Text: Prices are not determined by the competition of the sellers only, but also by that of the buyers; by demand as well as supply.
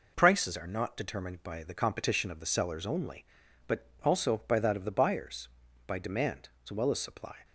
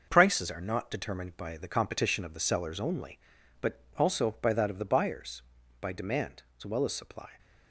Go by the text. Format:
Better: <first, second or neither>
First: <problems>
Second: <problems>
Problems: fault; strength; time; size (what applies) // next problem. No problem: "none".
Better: first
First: pauses between "but" and "also"; slight; at 3.8 s; 0.18 s long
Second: gets quieter; noticeable; throughout; 6 dB // pauses between "but" and "also"; slight; at 3.7 s; 0.18 s long